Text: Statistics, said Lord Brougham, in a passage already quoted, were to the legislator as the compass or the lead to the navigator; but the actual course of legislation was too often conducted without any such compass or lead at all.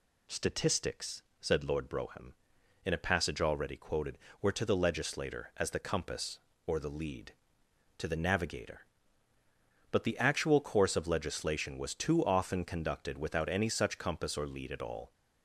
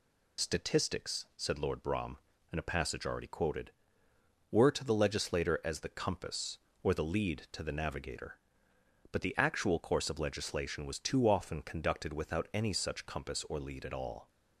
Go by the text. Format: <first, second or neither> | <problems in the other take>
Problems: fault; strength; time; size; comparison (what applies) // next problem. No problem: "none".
first | loses the start of "Statistics"; at 0.3 s; 35 ms